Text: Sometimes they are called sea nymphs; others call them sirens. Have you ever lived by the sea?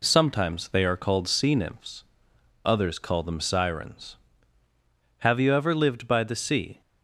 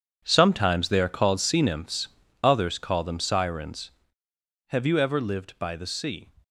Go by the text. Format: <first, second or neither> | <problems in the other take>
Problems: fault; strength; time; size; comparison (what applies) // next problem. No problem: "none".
first | gets quieter; strong; throughout; 13.5 dB